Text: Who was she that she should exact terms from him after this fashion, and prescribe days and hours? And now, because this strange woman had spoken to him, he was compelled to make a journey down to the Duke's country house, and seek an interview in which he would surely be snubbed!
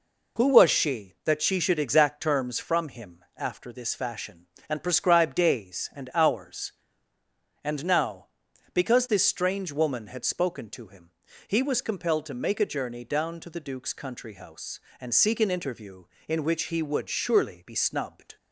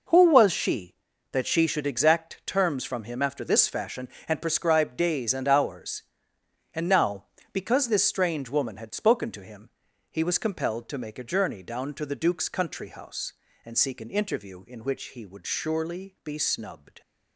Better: neither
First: none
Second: none

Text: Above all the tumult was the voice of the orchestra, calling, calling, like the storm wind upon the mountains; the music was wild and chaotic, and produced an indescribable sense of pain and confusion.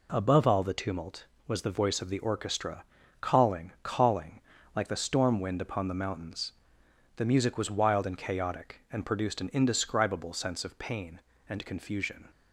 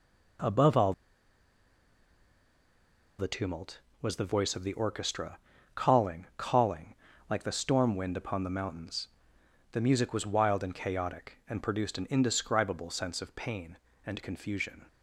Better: first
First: none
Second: pauses between "all" and "the"; strong; at 0.9 s; 2.2 s long

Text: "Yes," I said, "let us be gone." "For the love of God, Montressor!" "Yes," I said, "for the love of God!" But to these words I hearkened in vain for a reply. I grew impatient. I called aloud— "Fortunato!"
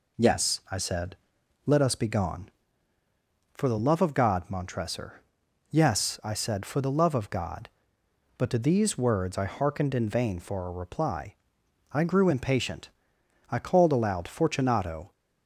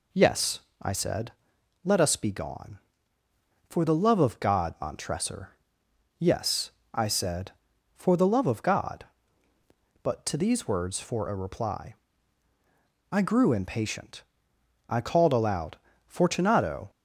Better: first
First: none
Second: skips "I hearkened in vain"; at 10.9 s

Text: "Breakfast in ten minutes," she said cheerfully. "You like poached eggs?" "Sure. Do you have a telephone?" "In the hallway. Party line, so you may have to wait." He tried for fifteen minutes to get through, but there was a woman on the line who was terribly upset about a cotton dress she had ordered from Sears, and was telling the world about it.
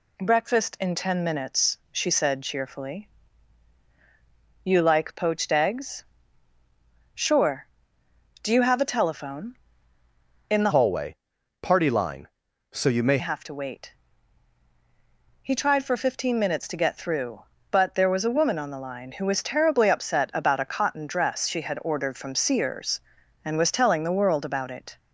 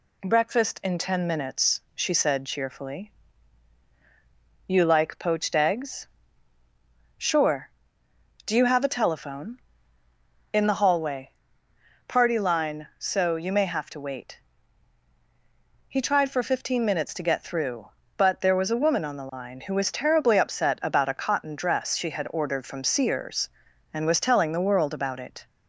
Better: second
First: changes voice from "hallway" to "may"; from 10.7 to 13.1 s; 2.4 s long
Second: none

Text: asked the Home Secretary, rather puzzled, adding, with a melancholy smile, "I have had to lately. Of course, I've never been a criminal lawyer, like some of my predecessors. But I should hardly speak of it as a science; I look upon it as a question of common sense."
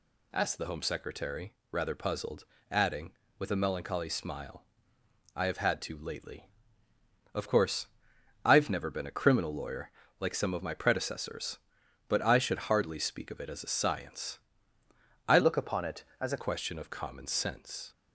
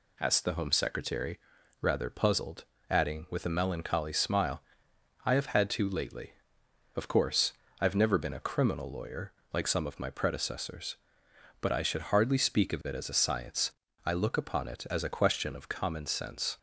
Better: second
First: changes voice from "look" to "a"; from 15.3 to 16.4 s; 1.1 s long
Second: none

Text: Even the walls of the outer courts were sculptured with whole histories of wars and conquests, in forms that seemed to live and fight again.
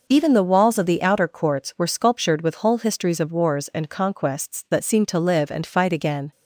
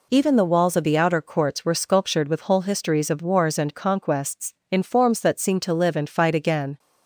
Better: second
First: skips "in forms"; at 4.6 s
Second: none

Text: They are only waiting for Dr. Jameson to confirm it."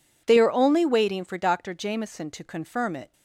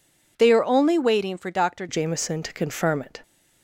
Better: first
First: none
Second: changes voice at "Jameson"; from 1.8 s on; 1.4 s long

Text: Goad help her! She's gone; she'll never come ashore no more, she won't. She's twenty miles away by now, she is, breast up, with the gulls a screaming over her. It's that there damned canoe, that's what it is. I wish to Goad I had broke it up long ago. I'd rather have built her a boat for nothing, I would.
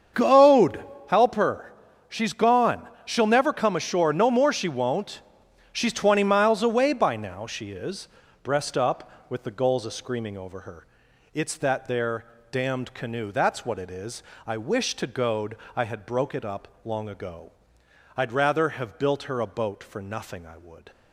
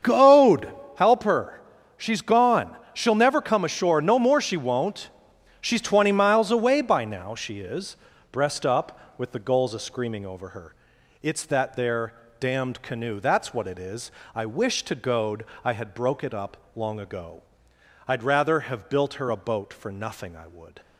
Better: neither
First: starts louder than the rest; strong; until 1.4 s; 7 dB // pauses between "Goad" and "help"; slight; at 0.8 s; 0.28 s long // pauses between "there" and "damned"; slight; at 12.2 s; 0.28 s long // pauses between "Goad" and "I"; slight; at 15.5 s; 0.18 s long // pauses between "up" and "long"; slight; at 16.6 s; 0.16 s long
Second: starts louder than the rest; strong; until 1.3 s; 7 dB // pauses between "Goad" and "help"; slight; at 0.6 s; 0.28 s long // pauses between "there" and "damned"; slight; at 12.1 s; 0.28 s long // pauses between "Goad" and "I"; slight; at 15.4 s; 0.18 s long // pauses between "up" and "long"; slight; at 16.5 s; 0.18 s long

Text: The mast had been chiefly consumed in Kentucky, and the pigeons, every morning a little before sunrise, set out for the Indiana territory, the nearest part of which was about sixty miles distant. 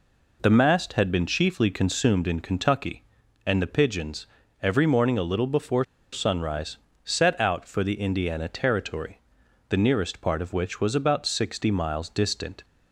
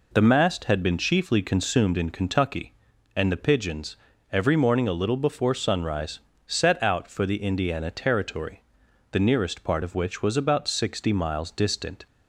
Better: second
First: pauses between "before" and "sunrise"; slight; at 5.8 s; 0.27 s long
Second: none

